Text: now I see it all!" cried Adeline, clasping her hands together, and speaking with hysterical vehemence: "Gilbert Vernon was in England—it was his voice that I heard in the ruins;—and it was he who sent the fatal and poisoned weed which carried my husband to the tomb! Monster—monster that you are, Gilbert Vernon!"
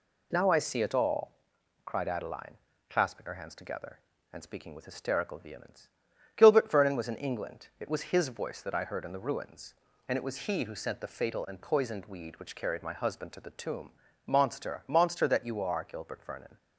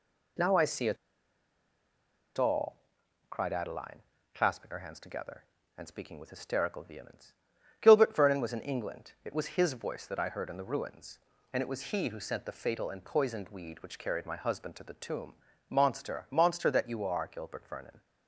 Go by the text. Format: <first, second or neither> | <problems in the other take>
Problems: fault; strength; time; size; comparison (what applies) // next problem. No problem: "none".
first | pauses between "it" and "all"; strong; at 0.9 s; 1.4 s long